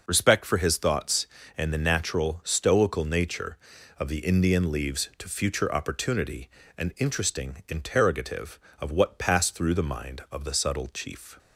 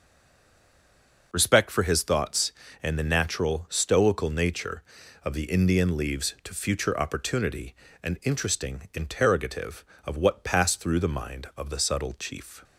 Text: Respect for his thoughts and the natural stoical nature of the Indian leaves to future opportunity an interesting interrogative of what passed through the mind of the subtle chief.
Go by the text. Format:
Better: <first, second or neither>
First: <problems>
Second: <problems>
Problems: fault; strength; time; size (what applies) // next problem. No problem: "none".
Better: first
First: pauses between "opportunity" and "an"; slight; at 6.4 s; 0.26 s long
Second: stays silent before the first word; noticeable; until 1.3 s; 1.3 s long // pauses between "opportunity" and "an"; slight; at 7.7 s; 0.26 s long